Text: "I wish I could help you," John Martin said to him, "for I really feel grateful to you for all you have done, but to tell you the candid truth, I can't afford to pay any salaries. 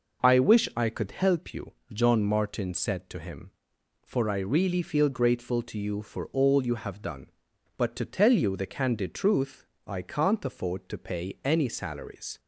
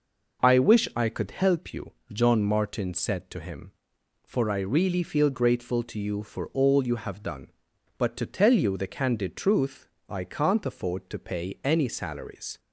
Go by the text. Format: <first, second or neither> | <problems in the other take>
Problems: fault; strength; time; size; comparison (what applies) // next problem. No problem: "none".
neither | none